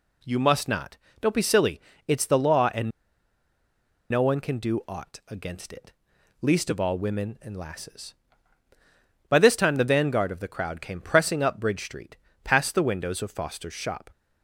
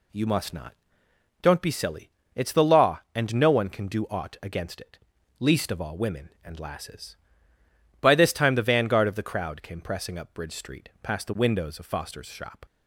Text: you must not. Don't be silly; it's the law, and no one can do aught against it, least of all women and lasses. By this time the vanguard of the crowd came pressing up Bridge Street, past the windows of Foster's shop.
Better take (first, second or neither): second